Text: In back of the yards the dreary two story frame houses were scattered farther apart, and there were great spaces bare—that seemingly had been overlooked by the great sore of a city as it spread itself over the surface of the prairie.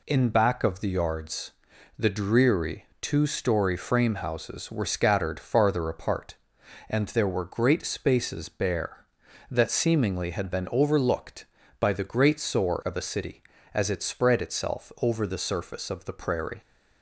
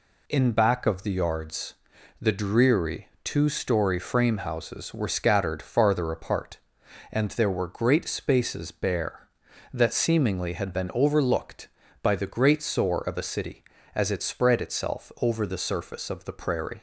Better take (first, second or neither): neither